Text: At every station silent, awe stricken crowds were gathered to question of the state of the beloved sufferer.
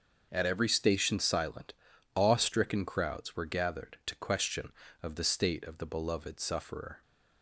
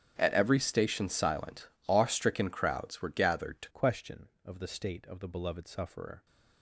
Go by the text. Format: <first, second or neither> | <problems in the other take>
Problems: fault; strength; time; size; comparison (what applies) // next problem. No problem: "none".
first | starts louder than the rest; strong; until 1.1 s; 9 dB; also in the first // changes voice at "question"; from 3.6 s on; 2.6 s long